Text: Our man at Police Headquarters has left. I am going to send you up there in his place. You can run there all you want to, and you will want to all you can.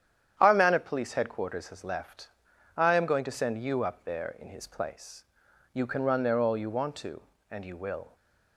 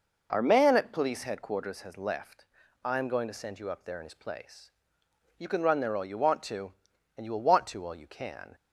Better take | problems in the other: second | starts louder than the rest; strong; until 1.4 s; 9.5 dB // stops before "want to all you can"; at 8.1 s

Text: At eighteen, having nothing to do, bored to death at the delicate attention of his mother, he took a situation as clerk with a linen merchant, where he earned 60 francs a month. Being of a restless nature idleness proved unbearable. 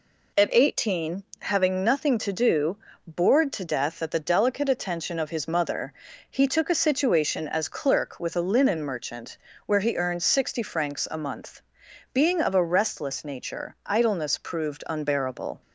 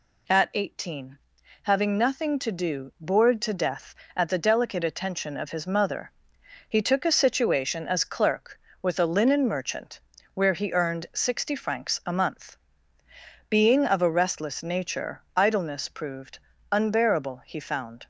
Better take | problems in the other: first | pauses between "nature" and "idleness"; slight; at 15.2 s; 0.16 s long // pauses between "proved" and "unbearable"; slight; at 16.3 s; 0.32 s long // goes on to say "He found"; noticeable; from 17.4 s on; 0.62 s long

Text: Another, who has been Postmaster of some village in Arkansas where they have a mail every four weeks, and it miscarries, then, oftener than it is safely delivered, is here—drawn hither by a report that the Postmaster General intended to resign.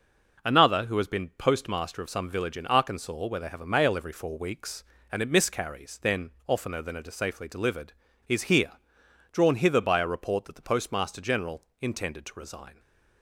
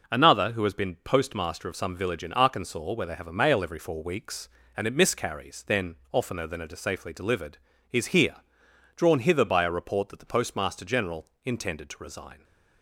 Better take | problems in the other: neither | pauses between "General" and "intended"; slight; the same in both

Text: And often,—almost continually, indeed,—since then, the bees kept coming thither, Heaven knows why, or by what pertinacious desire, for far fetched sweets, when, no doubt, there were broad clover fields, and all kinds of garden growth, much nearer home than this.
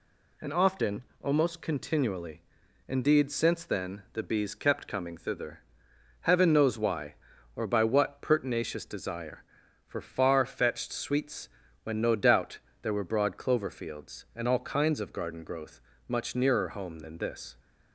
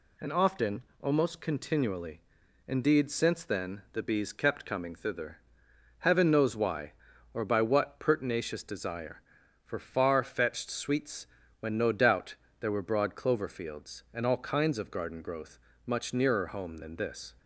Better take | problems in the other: neither | none

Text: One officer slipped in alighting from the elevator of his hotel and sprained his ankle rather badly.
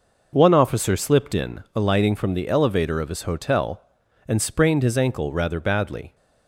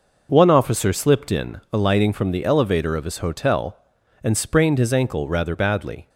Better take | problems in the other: neither | none

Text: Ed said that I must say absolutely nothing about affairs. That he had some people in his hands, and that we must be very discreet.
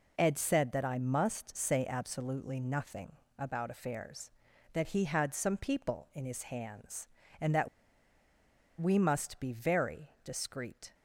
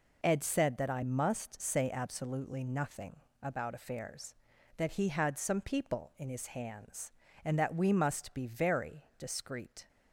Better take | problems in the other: second | pauses between "nothing" and "about"; slight; at 3.1 s; 0.26 s long; slight in the second // pauses between "that" and "we"; at 7.6 s; 1.1 s long

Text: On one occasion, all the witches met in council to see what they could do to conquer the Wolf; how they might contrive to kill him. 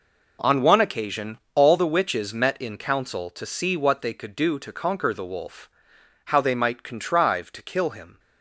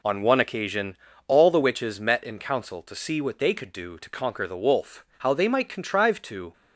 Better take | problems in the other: first | stops before "kill him"; at 6.5 s

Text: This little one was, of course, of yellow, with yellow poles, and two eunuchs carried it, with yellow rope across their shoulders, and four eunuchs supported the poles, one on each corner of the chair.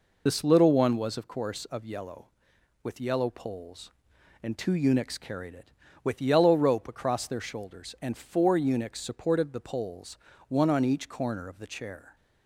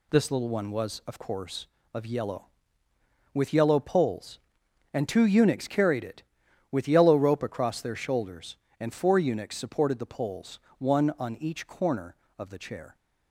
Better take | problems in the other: second | loses the start of "This"; at 0.2 s; 45 ms

